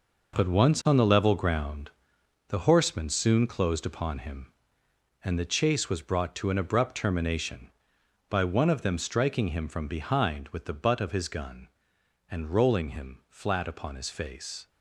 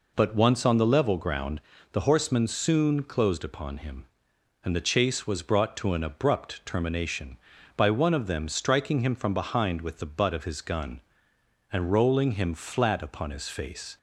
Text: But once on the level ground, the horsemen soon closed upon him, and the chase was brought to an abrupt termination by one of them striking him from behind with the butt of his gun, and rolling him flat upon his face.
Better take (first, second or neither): second